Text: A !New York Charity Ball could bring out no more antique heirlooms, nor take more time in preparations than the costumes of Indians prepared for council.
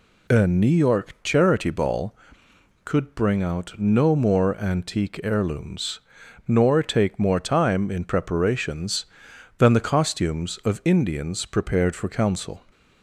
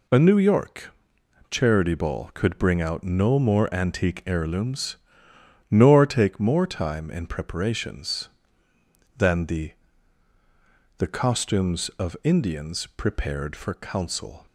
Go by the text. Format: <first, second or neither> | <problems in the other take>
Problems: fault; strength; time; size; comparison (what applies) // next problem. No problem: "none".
first | pauses between "York" and "Charity"; noticeable; at 0.9 s; 0.56 s long // says "the" twice; at 10.9 s